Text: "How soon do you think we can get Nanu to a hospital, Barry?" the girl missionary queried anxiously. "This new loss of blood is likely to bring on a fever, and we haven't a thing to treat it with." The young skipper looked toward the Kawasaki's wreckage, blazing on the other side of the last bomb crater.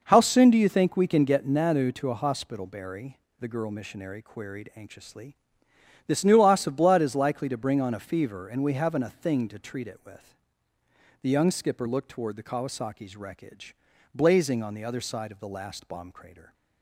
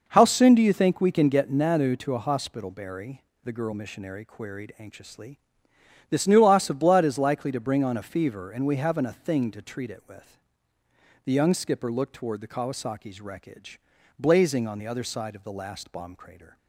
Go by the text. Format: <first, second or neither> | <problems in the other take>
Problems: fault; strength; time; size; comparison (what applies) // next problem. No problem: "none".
neither | none